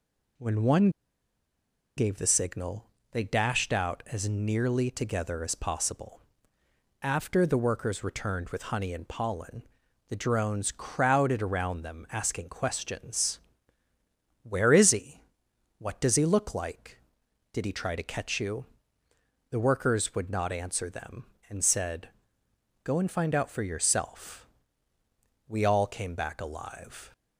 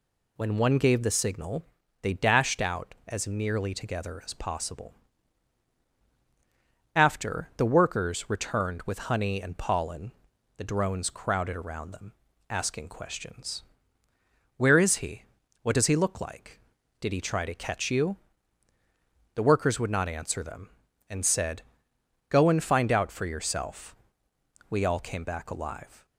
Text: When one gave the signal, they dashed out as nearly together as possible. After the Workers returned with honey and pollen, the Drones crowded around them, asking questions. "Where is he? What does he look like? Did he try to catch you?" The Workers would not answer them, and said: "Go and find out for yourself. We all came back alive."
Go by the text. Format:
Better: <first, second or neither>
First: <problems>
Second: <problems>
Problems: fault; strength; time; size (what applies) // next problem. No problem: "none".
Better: second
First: pauses between "one" and "gave"; at 0.8 s; 1.0 s long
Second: none